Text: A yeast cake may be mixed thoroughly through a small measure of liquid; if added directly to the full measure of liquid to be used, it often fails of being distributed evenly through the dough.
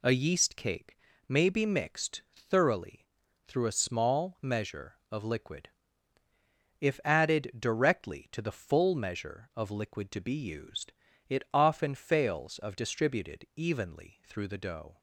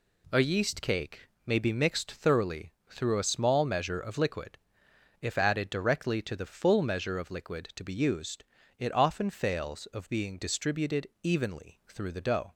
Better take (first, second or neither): second